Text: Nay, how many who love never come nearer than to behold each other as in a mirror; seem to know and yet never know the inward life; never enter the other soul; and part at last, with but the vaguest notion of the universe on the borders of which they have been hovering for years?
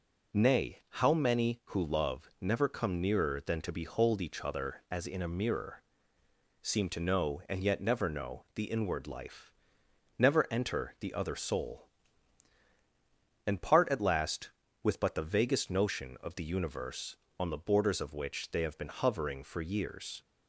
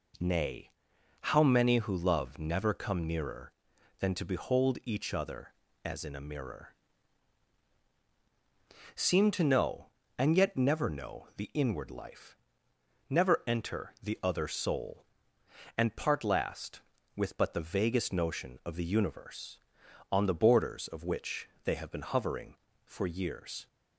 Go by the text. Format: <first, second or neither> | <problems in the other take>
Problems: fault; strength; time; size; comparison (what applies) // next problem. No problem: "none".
first | skips "at"; at 16.2 s // pauses between "which" and "they"; slight; at 21.4 s; 0.16 s long